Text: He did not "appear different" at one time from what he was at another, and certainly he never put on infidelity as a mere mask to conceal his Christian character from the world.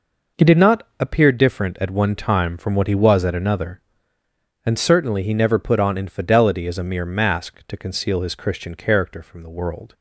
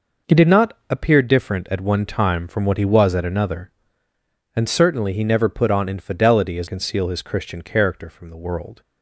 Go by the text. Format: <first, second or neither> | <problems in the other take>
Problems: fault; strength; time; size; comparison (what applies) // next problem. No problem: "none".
first | skips "a mere mask to"; at 6.6 s